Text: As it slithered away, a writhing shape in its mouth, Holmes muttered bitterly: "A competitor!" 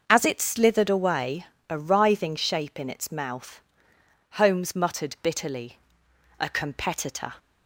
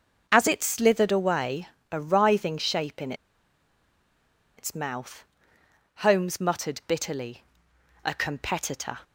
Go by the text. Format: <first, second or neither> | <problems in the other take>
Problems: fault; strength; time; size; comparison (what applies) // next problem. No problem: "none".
first | starts louder than the rest; until 1.3 s; 6 dB; also in the first // pauses between "in" and "its"; strong; at 3.1 s; 1.4 s long